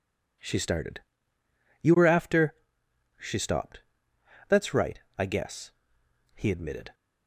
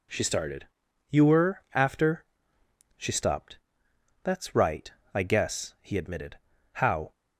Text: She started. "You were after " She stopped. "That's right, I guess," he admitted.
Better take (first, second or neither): first